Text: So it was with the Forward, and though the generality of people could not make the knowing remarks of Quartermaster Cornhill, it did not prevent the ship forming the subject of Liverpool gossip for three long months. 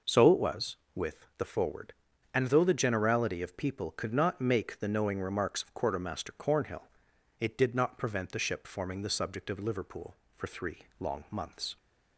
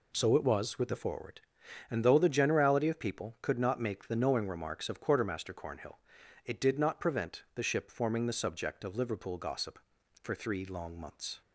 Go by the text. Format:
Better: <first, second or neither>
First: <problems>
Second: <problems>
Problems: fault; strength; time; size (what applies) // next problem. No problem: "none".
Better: second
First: skips "gossip"; at 10.2 s // pauses between "three" and "long"; slight; at 10.7 s; 0.20 s long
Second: none